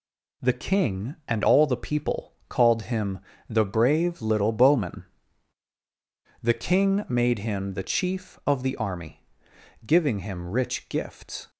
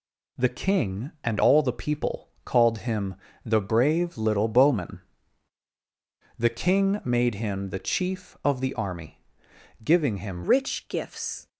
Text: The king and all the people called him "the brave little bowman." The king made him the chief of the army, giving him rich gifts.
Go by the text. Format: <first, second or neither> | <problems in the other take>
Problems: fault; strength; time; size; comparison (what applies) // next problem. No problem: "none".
first | pauses between "people" and "called"; slight; at 2.2 s; 0.16 s long; slight in the first // pauses between "him" and "the"; slight; at 3.1 s; 0.28 s long; slight in the first // changes voice at "rich"; from 10.4 s on; 1.0 s long